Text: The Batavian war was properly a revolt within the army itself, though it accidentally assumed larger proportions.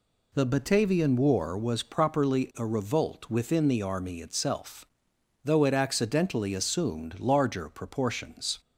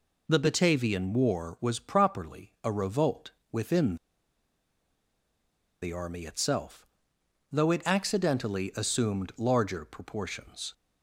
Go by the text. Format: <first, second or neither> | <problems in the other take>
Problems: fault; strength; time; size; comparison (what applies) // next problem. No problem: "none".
first | pauses between "revolt" and "within"; slight; at 3.3 s; 0.20 s long // pauses between "within" and "the"; strong; at 3.9 s; 1.8 s long